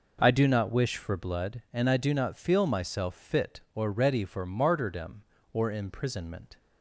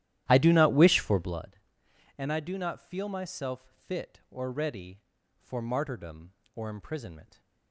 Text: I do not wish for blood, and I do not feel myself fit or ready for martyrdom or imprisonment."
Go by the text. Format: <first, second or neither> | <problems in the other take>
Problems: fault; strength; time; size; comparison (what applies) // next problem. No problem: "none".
first | starts louder than the rest; strong; until 1.5 s; 13 dB